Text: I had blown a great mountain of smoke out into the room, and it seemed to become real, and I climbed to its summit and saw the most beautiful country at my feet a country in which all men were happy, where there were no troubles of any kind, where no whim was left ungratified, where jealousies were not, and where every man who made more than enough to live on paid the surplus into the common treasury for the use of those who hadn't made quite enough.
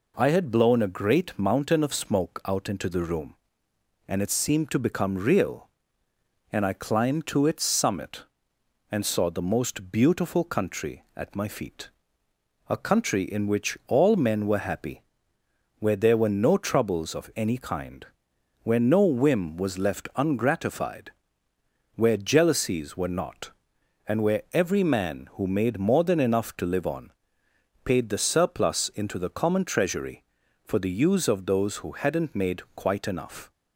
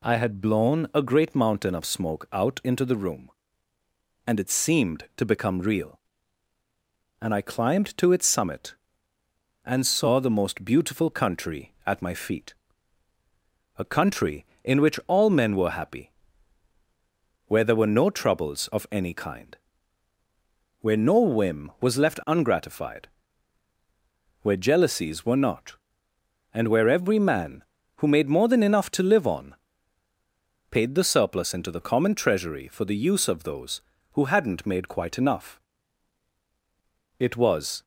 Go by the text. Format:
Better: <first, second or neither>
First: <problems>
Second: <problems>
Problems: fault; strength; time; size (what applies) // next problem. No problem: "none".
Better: first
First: pauses between "feet" and "a"; noticeable; at 11.9 s; 0.78 s long // pauses between "on" and "paid"; noticeable; at 27.1 s; 0.72 s long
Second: pauses between "feet" and "a"; strong; at 12.5 s; 1.2 s long // pauses between "on" and "paid"; at 29.5 s; 1.1 s long // goes on to say "It was"; noticeable; from 37.1 s on; 0.64 s long